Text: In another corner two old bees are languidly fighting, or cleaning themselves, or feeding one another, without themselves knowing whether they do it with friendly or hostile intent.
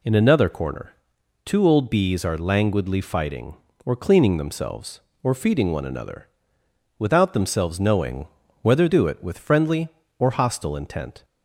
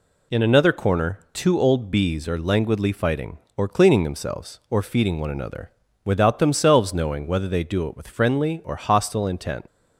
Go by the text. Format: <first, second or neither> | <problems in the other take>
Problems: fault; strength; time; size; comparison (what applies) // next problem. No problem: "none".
second | pauses between "corner" and "two"; noticeable; at 0.9 s; 0.50 s long // pauses between "knowing" and "whether"; slight; at 8.2 s; 0.36 s long // skips "they"; at 8.8 s